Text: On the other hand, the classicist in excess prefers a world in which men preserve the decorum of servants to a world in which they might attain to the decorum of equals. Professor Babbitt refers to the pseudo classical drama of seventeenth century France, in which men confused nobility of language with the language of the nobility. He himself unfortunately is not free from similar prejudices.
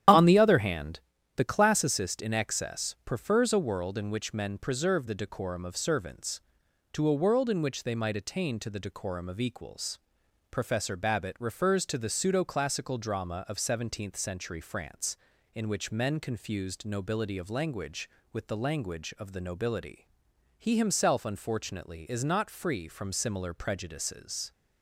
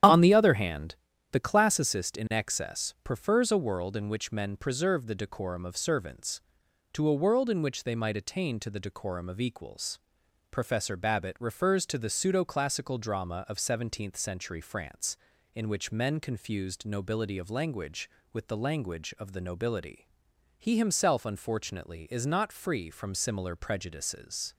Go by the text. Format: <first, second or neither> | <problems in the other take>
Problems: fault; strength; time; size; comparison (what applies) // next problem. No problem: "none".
neither | starts louder than the rest; strong; the same in both